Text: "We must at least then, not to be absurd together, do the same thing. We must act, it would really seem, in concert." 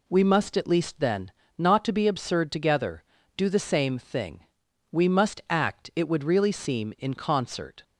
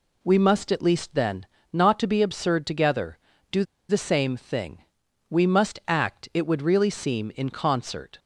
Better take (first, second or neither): first